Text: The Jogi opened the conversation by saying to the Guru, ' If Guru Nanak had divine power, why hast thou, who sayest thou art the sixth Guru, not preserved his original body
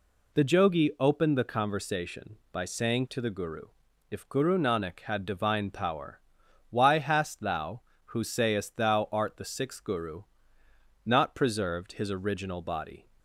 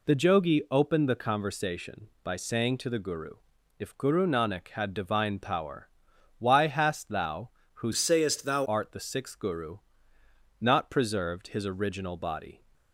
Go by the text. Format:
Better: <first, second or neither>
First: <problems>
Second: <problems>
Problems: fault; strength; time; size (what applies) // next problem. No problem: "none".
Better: first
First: none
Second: changes voice from "sayest" to "thou"; from 7.9 to 8.6 s; 0.7 s long